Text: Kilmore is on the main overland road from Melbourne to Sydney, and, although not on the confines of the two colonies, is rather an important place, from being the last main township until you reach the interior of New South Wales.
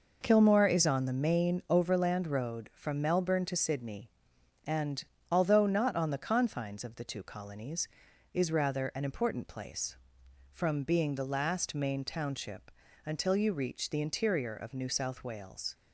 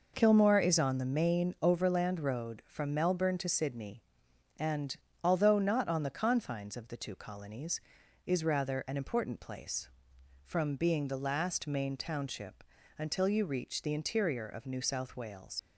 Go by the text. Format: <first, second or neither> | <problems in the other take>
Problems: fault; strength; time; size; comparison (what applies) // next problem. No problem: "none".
first | pauses between "township" and "until"; slight; at 12.6 s; 0.34 s long; slight in the first // leaves "Wales" unfinished; at 15.5 s; 70 ms